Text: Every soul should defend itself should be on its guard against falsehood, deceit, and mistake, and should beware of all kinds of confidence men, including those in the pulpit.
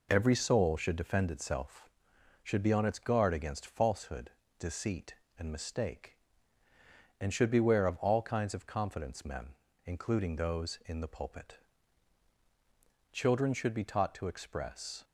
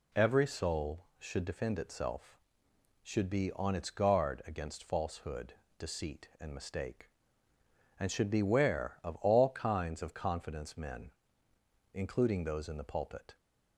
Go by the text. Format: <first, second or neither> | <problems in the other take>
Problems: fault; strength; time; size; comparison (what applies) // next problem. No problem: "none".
second | goes on to say "Children should be taught to express"; strong; from 13.1 s on; 1.9 s long